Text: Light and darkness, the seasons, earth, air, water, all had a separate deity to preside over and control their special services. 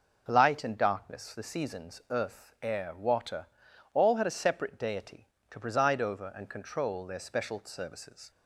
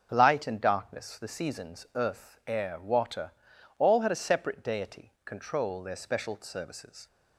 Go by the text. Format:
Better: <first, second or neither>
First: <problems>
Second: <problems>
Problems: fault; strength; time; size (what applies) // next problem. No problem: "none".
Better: first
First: none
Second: starts louder than the rest; until 1.1 s; 6 dB // skips "to preside over and"; at 5.1 s